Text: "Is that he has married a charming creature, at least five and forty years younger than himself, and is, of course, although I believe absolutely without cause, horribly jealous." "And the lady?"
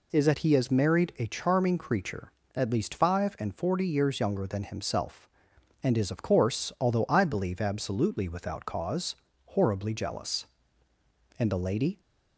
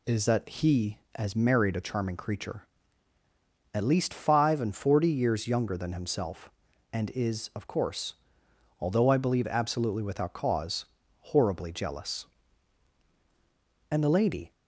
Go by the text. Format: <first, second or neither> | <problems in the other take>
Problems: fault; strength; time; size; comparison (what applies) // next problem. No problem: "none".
neither | none